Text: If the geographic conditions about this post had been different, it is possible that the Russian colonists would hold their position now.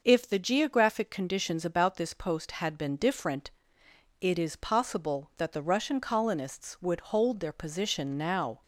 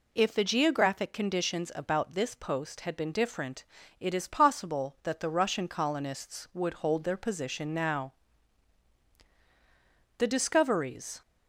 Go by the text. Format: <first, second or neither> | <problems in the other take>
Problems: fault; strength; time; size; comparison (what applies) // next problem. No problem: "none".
first | goes on to say "The discoveries"; noticeable; from 10.1 s on; 1.0 s long